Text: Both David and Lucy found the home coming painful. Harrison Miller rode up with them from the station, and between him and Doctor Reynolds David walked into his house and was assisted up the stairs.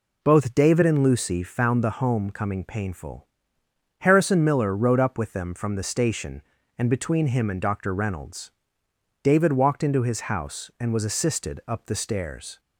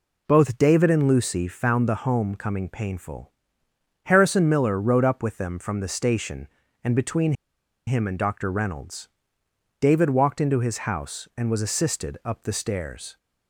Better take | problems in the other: first | pauses between "between" and "him"; noticeable; at 7.3 s; 0.54 s long // pauses between "Reynolds" and "David"; noticeable; at 9.0 s; 0.72 s long; noticeable in the first

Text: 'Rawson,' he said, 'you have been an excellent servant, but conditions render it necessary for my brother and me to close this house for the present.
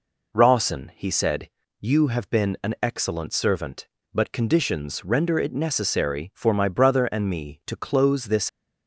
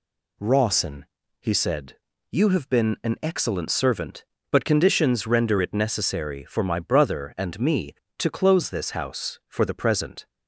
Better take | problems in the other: second | stops before "house for the present"; at 8.4 s

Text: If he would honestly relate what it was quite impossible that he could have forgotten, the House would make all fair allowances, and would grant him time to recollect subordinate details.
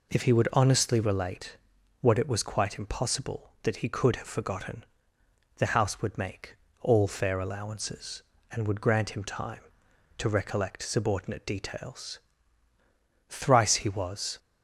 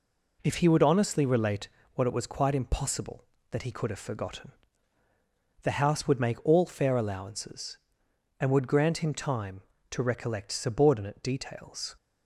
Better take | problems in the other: second | pauses between "relate" and "what"; at 1.5 s; 0.44 s long; slight in the second // pauses between "make" and "all"; slight; at 6.5 s; 0.24 s long // goes on to say "Thrice he was"; noticeable; from 13.2 s on; 1.1 s long

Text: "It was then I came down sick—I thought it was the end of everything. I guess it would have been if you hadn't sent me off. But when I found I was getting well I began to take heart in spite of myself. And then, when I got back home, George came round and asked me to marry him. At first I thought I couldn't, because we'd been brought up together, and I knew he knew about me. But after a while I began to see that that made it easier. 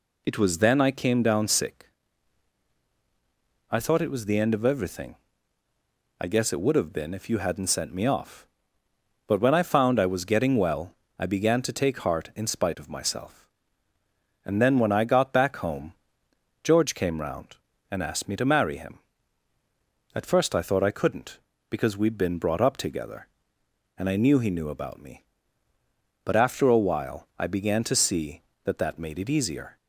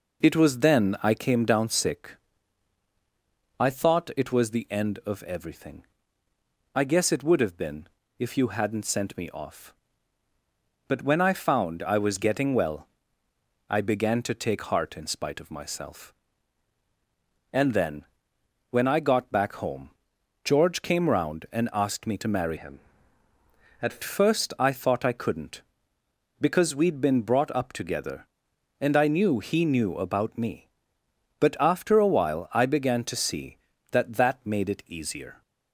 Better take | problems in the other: first | pauses between "been" and "if"; slight; at 7.8 s; 0.32 s long // pauses between "well" and "I"; noticeable; at 12.8 s; 0.80 s long; slight in the first // changes voice from "him" to "At"; from 22.5 to 24.0 s; 1.5 s long

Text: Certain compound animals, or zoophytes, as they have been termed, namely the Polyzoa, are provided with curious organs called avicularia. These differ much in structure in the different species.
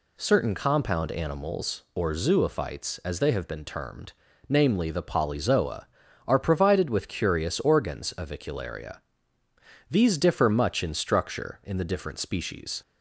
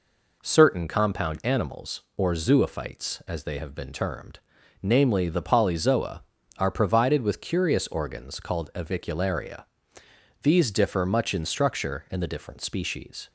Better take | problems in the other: second | skips "called"; at 8.1 s

